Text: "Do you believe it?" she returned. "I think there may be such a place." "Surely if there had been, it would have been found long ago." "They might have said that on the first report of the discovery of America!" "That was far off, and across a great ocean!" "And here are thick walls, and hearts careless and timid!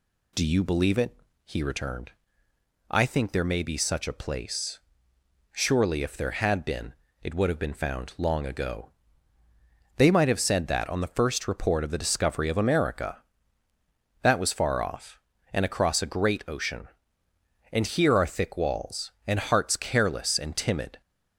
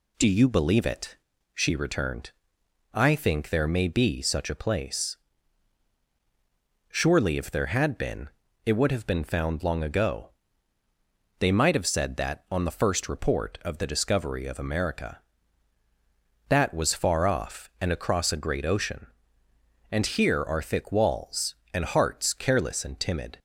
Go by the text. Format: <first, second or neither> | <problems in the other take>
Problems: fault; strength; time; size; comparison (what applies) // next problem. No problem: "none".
second | says "he" for "she"; at 1.4 s